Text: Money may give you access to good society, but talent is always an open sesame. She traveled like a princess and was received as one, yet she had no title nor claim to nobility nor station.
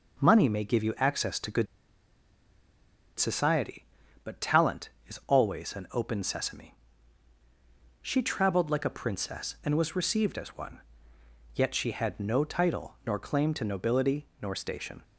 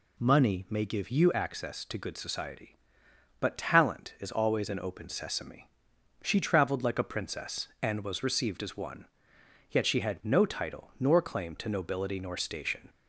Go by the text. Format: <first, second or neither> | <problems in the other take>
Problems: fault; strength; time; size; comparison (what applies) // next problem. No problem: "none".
second | pauses between "good" and "society"; strong; at 1.6 s; 1.5 s long // pauses between "nobility" and "nor"; slight; at 14.2 s; 0.16 s long